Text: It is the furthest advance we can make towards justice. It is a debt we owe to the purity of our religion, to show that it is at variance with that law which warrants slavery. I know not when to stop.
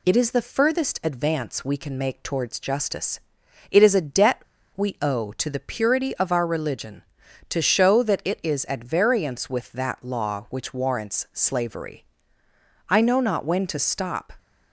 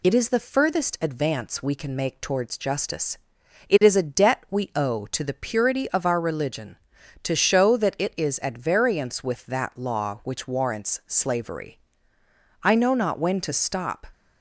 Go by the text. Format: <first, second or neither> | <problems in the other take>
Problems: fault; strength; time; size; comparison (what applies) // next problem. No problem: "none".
second | pauses between "debt" and "we"; slight; at 4.4 s; 0.33 s long